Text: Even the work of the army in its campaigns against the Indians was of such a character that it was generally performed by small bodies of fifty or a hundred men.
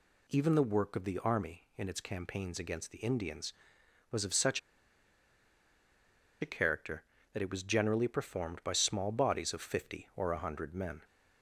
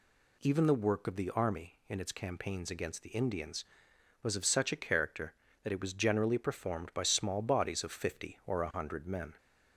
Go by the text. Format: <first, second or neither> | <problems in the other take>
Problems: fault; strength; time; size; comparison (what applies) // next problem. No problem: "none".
second | pauses between "such" and "a"; strong; at 4.5 s; 1.8 s long